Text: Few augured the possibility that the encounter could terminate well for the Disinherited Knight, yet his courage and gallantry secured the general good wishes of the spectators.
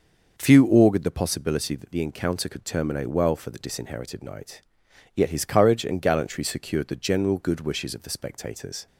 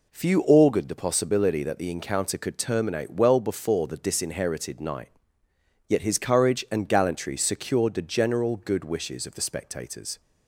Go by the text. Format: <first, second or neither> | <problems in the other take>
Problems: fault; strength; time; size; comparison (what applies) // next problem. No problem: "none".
first | says "before" for "for"; at 3.4 s